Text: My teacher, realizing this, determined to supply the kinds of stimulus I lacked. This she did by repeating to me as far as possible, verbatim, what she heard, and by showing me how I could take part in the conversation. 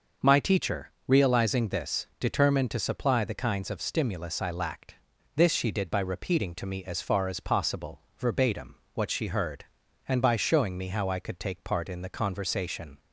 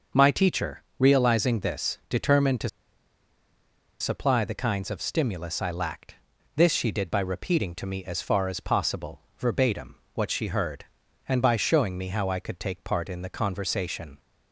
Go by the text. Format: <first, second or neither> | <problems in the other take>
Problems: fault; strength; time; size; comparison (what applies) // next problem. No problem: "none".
first | starts louder than the rest; until 1.3 s; 6 dB; noticeable in the first // pauses between "to" and "supply"; strong; at 2.6 s; 1.3 s long